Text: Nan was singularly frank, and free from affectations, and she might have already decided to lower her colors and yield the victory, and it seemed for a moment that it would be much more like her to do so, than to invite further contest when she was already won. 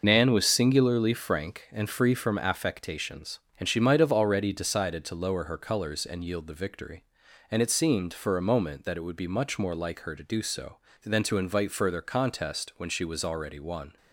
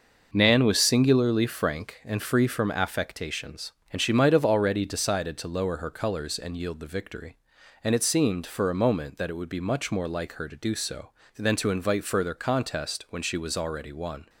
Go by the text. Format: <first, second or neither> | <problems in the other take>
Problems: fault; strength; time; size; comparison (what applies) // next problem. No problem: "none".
second | loses the start of "Nan"; at 0.0 s; 30 ms